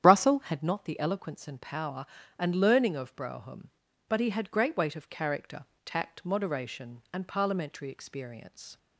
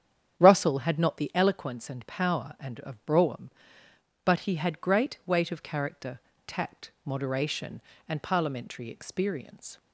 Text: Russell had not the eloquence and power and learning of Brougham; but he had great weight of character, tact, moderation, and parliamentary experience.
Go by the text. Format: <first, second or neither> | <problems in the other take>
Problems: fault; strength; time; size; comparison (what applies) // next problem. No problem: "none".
first | starts louder than the rest; strong; until 1.4 s; 9 dB; strong in the first // skips "learning"; at 2.7 s